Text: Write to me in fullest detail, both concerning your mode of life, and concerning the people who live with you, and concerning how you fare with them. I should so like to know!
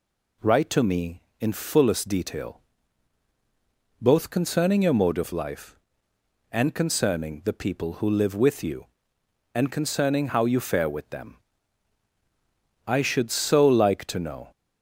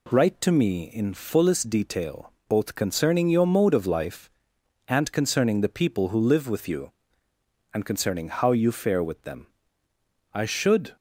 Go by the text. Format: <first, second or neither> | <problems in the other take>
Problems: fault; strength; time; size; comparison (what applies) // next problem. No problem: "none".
first | stops before "so like to know"; at 10.9 s